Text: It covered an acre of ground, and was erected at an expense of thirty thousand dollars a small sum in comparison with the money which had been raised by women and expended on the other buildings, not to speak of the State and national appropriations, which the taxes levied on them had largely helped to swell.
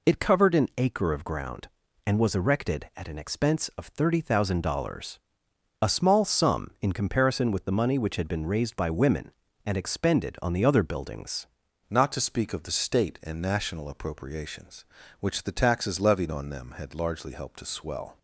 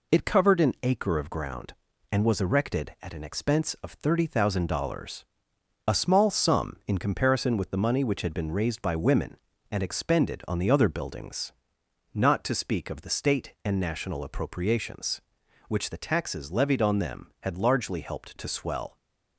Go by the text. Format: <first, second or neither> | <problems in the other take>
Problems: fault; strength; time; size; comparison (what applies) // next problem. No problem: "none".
second | pauses between "dollars" and "a"; noticeable; at 5.1 s; 0.64 s long; noticeable in the second // changes voice at "not"; from 11.8 s on; 6.3 s long